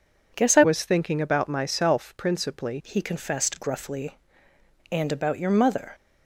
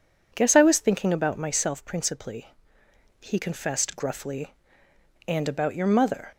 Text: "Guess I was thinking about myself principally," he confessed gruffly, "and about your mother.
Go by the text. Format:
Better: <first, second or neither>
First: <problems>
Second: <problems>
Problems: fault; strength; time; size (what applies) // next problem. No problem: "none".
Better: second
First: changes voice from "was" to "principally"; from 0.6 to 2.7 s; 2.1 s long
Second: none